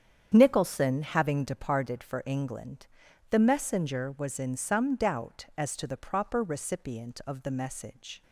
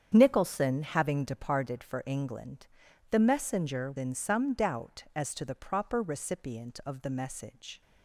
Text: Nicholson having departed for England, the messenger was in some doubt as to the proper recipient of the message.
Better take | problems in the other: first | starts louder than the rest; strong; until 1.1 s; 8.5 dB; strong in the first // skips "was"; at 3.9 s

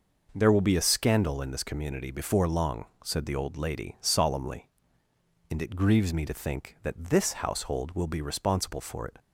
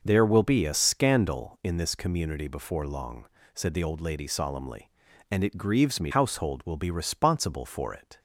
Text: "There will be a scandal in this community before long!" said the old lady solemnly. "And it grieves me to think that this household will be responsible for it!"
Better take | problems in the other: first | skips "to think that this"; at 6.1 s

